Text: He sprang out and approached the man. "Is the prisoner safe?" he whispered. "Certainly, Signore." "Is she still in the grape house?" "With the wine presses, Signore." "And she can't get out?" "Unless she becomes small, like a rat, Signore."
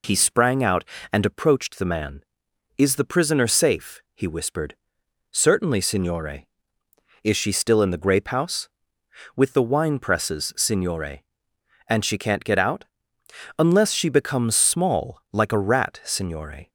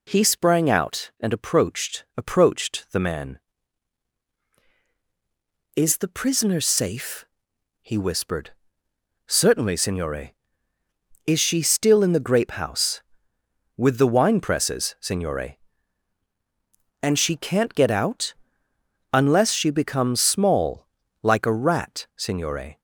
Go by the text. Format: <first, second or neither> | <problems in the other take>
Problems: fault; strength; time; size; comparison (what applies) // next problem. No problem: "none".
first | says "approached" twice; at 2.1 s